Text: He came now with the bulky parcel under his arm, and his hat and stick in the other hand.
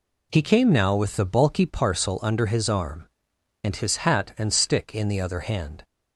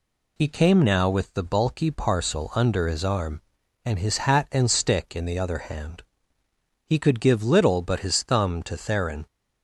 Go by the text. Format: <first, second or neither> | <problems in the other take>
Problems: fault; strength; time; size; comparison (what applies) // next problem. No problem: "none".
first | goes on to say "He could give little but his thumb to Theron"; strong; from 6.8 s on; 2.4 s long